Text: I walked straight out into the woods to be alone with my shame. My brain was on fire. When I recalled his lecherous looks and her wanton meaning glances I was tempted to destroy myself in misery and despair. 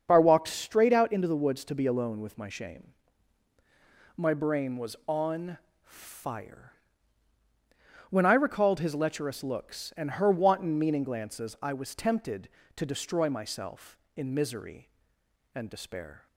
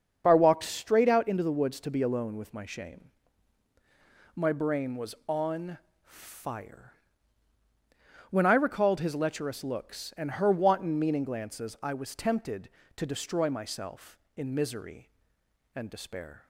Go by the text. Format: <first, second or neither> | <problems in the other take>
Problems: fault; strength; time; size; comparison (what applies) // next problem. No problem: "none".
neither | starts louder than the rest; the same in both // pauses between "on" and "fire"; slight; the same in both